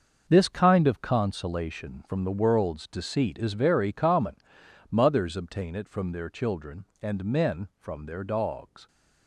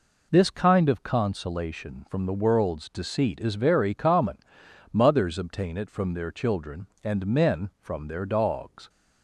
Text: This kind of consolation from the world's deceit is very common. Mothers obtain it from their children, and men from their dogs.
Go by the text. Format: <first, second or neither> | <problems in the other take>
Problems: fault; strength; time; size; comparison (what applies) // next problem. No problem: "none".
second | gets quieter; strong; throughout; 9.5 dB